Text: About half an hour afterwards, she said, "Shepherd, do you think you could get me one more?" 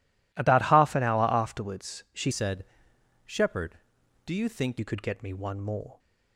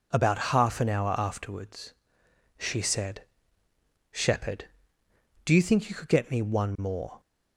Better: second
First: changes voice from "said" to "think"; from 2.3 to 4.7 s; 2.4 s long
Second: none

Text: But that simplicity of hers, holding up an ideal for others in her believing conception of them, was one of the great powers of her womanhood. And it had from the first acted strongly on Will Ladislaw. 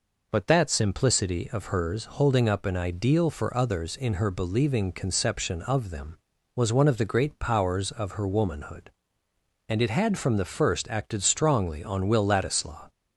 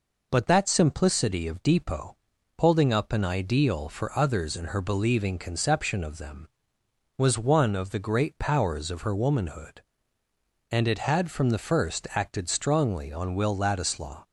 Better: first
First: none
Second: says "depot" for "hers"; at 1.6 s

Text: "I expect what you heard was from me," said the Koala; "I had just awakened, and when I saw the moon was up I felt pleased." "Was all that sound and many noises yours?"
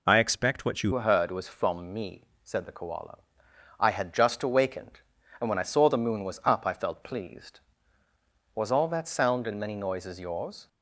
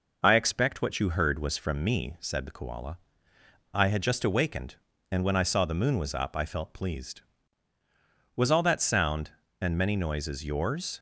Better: second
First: changes voice at "heard"; from 0.9 s on; 9.7 s long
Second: none

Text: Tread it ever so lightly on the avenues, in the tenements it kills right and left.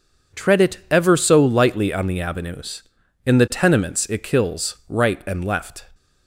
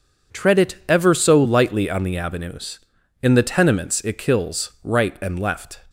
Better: neither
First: none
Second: none

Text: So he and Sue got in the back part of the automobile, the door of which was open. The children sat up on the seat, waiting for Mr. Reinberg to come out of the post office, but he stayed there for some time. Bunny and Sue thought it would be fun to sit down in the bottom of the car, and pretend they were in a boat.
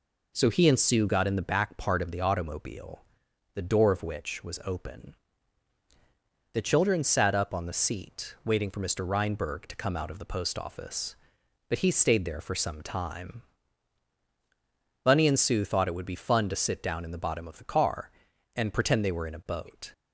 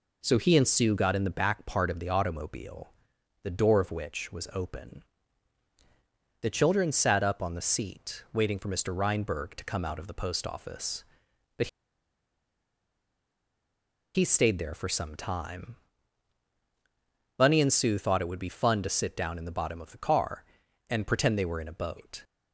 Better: first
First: none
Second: pauses between "but" and "he"; strong; at 11.6 s; 2.4 s long

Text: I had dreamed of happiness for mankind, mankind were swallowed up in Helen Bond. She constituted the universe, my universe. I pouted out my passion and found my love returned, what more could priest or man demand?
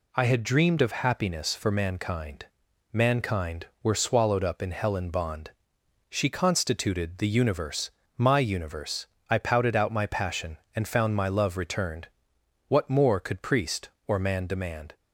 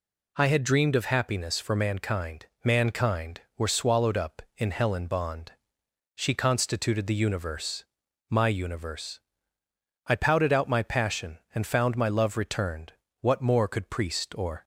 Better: first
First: none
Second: stops before "man demand"; at 14.6 s

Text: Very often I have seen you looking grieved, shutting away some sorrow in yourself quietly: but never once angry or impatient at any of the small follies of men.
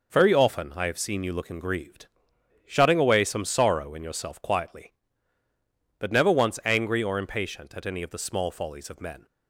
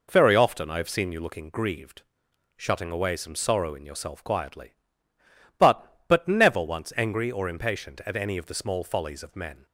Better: first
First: none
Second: says "but" twice; at 6.0 s

